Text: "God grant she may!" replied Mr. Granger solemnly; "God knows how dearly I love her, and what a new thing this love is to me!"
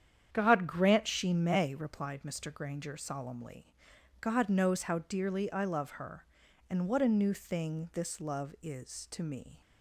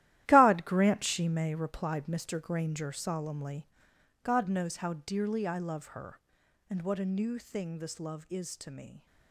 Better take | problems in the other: first | gets quieter; strong; throughout; 12 dB // starts louder than the rest; strong; until 1.2 s; 14 dB; strong in the first

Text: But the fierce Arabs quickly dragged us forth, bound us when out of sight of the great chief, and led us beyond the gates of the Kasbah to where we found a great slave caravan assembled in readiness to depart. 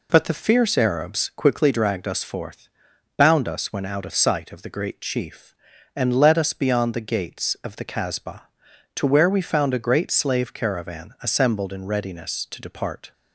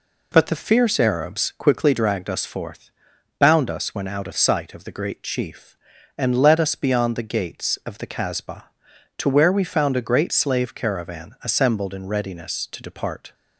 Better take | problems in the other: neither | none

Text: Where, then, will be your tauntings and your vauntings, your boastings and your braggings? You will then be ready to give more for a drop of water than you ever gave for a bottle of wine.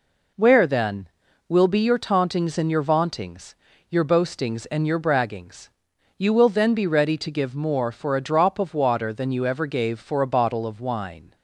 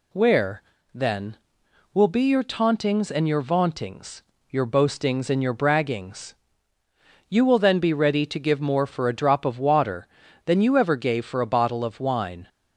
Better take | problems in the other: neither | none

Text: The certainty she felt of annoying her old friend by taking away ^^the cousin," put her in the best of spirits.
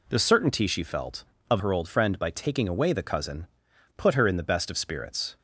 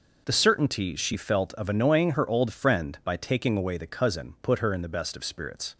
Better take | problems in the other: second | skips "annoying"; at 1.5 s

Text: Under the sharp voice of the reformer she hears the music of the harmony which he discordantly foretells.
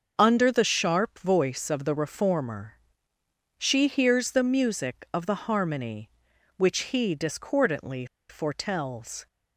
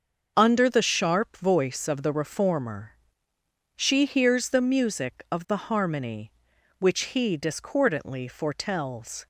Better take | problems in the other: second | starts louder than the rest; until 1.1 s; 6 dB; also in the second // pauses between "reformer" and "she"; noticeable; at 2.7 s; 0.82 s long; noticeable in the second // pauses between "discordantly" and "foretells"; slight; at 8.0 s; 0.24 s long

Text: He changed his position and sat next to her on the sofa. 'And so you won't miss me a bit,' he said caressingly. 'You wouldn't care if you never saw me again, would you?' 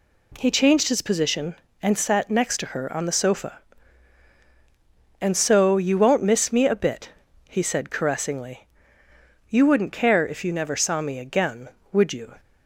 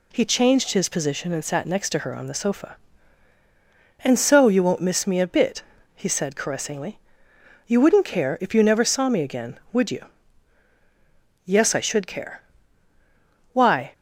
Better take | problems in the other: first | goes on to say "Yes I should care Why"; strong; from 11.4 s on; 2.4 s long

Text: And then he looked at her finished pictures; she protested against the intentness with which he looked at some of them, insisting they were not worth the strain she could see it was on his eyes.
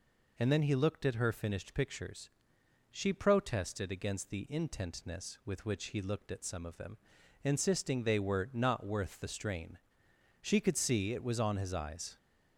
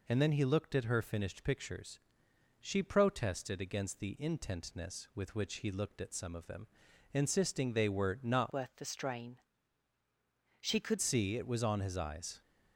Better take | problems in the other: first | changes voice from "worth" to "could"; from 8.5 to 10.9 s; 2.4 s long // pauses between "strain" and "she"; at 9.3 s; 1.2 s long; noticeable in the first

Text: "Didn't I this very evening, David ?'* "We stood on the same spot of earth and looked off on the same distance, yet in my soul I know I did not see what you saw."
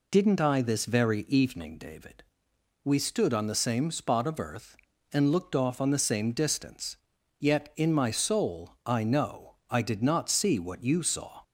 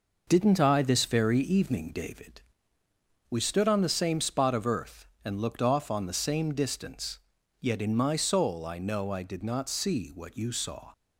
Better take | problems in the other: neither | none

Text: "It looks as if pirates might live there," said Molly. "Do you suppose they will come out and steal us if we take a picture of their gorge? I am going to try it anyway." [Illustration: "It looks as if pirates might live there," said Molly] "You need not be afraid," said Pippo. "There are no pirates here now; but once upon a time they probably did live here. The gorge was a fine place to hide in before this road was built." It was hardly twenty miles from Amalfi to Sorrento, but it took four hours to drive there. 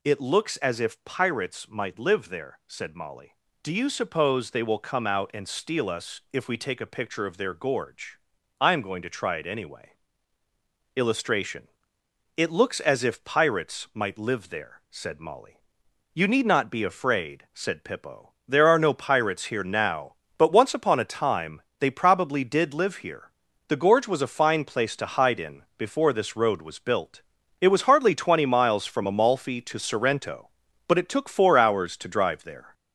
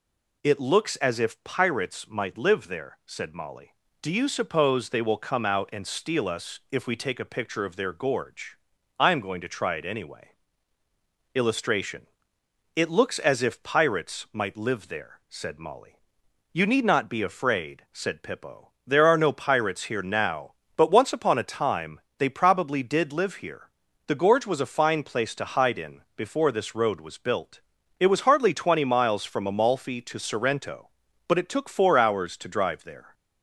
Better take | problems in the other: second | gets louder; noticeable; throughout; 5.5 dB // pauses between "Molly" and "You"; noticeable; at 15.6 s; 0.54 s long; noticeable in the second // pauses between "time" and "they"; slight; at 21.6 s; 0.18 s long; slight in the second

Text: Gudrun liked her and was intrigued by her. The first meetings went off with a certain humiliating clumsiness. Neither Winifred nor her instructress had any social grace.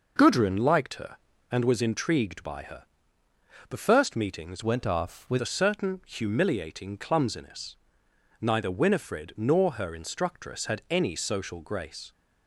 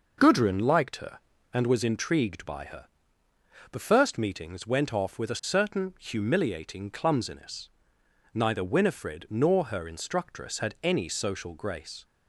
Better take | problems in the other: second | changes voice from "went" to "with"; from 4.6 to 5.3 s; 0.7 s long

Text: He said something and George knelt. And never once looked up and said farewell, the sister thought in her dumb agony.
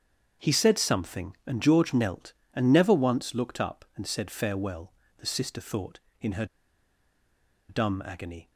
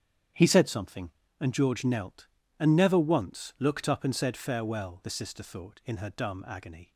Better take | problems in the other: second | starts louder than the rest; strong; until 1.5 s; 7.5 dB; strong in the second // pauses between "her" and "dumb"; at 6.4 s; 1.2 s long

